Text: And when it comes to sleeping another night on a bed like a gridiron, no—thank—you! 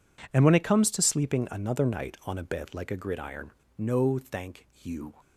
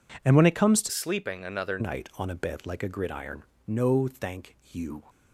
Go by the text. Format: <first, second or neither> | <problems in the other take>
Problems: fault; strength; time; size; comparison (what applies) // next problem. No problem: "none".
first | changes voice from "sleeping" to "another"; from 0.8 to 1.7 s; 0.9 s long